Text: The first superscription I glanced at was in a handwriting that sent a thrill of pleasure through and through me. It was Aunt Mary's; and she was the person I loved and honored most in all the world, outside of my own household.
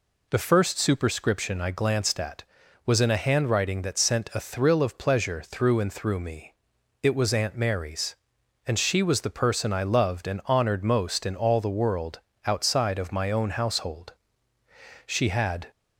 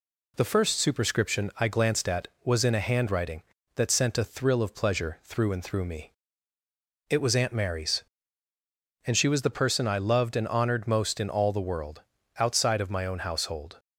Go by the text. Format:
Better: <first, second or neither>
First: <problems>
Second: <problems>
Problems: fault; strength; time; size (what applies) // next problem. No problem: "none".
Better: second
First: goes on to say "She had"; noticeable; from 15.0 s on; 0.62 s long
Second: none